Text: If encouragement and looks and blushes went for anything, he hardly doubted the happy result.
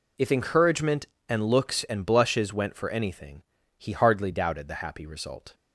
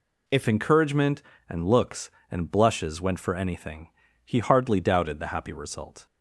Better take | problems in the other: first | changes voice at "encouragement"; from 0.4 s on; 5.6 s long

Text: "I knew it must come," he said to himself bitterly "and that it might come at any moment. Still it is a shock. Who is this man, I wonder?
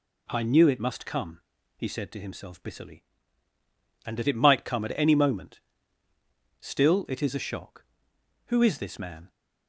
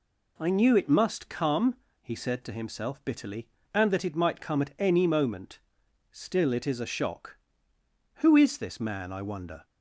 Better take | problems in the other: second | stops before "I wonder"; at 9.2 s

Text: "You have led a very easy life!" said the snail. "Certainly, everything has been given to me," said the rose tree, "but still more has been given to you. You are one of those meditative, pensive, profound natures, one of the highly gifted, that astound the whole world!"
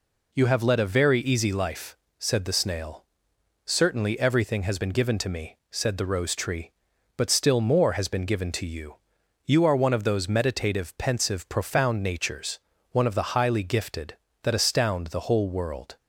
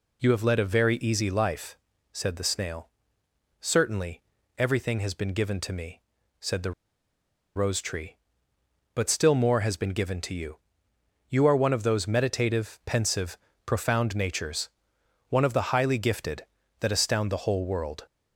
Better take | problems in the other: first | pauses between "the" and "rose"; noticeable; at 6.7 s; 0.84 s long

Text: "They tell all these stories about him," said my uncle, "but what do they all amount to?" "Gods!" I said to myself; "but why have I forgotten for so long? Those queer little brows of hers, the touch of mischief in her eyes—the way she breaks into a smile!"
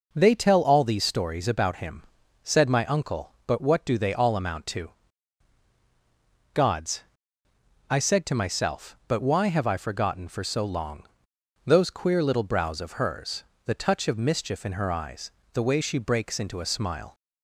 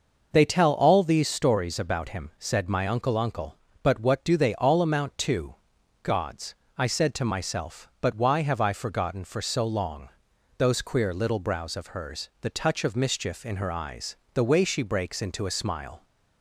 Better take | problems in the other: first | says "uncle" twice; at 3.1 s

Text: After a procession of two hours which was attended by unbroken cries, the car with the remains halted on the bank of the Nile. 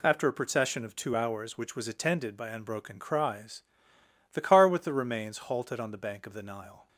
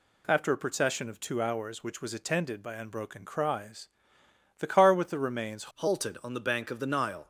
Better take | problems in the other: first | changes voice at "halted"; from 5.7 s on; 1.5 s long

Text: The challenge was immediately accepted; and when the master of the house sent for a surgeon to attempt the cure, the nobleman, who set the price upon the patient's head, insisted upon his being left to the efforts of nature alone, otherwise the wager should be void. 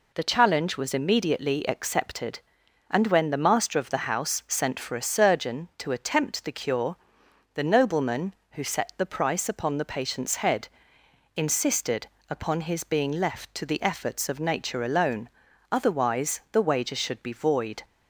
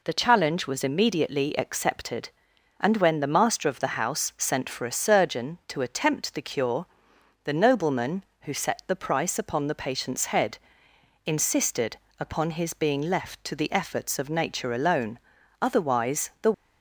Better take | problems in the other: first | pauses between "insisted" and "upon"; slight; at 11.9 s; 0.20 s long; slight in the first // stops before "wager should be void"; at 16.5 s

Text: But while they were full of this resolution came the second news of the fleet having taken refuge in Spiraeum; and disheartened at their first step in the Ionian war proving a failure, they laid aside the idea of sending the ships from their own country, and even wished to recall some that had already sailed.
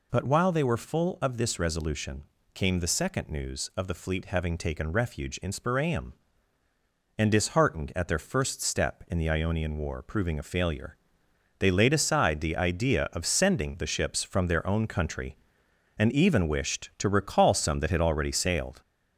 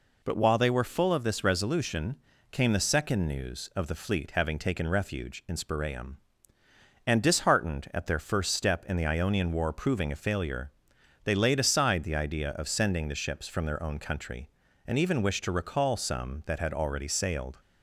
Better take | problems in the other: second | gets louder; noticeable; throughout; 4 dB // pauses between "resolution" and "came"; slight; at 2.2 s; 0.28 s long; slight in the second

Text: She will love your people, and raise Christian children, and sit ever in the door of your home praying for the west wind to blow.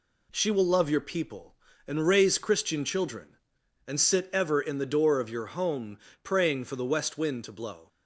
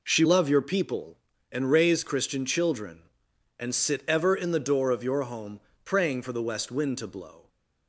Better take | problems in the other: first | skips "will"; at 0.2 s // pauses between "home" and "praying"; slight; at 5.6 s; 0.24 s long; slight in the first

